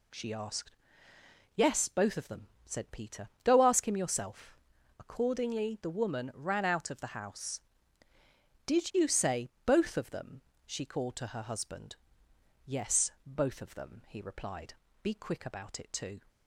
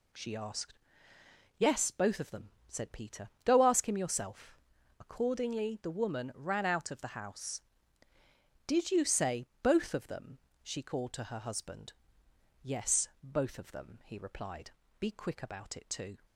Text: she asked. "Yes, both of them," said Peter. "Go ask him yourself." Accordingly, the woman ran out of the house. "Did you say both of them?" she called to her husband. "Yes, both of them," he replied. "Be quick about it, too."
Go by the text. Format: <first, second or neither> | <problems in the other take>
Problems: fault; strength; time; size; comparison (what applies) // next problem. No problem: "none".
neither | pauses between "say" and "both"; slight; the same in both